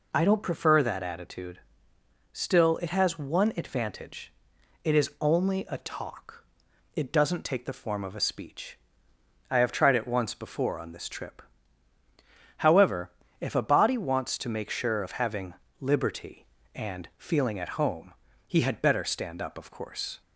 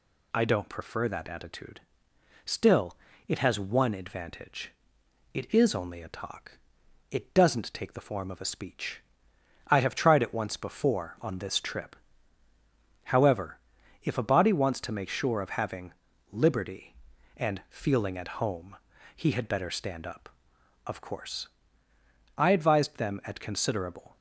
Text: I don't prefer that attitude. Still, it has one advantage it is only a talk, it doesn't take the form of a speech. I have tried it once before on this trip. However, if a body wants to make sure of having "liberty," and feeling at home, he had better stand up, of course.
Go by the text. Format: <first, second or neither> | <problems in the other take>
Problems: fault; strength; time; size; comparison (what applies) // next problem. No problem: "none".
first | pauses between "advantage" and "it"; noticeable; at 4.7 s; 0.58 s long; noticeable in the first // pauses between "having" and "liberty"; at 15.9 s; 0.38 s long; slight in the first // goes on to say "I advised them at considerable"; strong; from 22.3 s on; 1.8 s long